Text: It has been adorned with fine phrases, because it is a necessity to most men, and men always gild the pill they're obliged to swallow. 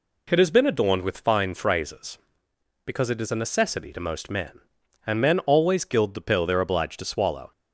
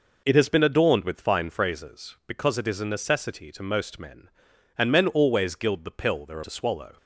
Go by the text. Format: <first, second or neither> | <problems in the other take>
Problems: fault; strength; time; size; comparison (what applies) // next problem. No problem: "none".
first | skips "obliged"; at 6.4 s